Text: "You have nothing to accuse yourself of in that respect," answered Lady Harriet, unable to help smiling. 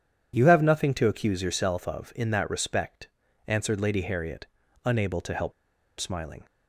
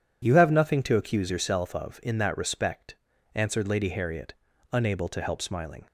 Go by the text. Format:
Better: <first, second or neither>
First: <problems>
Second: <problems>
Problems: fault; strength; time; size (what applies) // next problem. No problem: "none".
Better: second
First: pauses between "help" and "smiling"; noticeable; at 5.5 s; 0.46 s long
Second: none